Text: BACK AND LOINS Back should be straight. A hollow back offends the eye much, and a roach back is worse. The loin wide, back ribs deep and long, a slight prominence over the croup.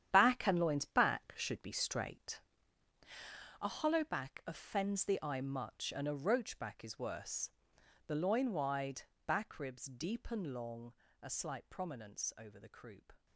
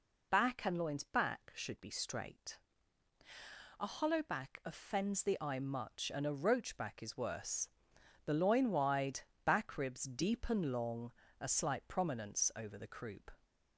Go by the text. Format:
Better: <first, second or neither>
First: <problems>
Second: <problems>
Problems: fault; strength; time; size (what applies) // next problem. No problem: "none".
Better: second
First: gets quieter; strong; throughout; 10 dB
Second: none